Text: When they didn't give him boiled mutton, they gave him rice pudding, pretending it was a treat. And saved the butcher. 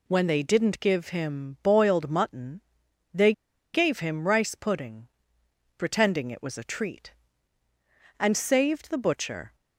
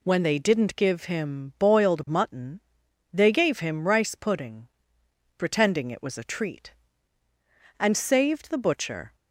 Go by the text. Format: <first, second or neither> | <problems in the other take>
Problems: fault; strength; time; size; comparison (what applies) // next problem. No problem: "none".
second | pauses between "they" and "gave"; at 3.3 s; 0.42 s long